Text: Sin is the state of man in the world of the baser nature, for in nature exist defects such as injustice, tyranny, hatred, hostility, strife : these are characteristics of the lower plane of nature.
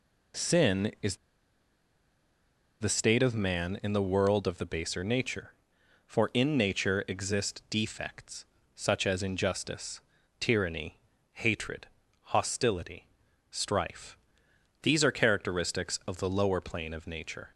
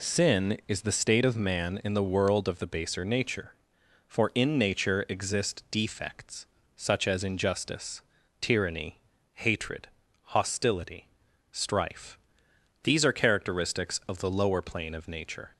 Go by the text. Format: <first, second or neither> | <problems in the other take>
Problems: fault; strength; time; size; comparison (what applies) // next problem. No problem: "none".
second | pauses between "is" and "the"; strong; at 1.1 s; 1.6 s long // pauses between "defects" and "such"; slight; at 8.4 s; 0.32 s long; slight in the second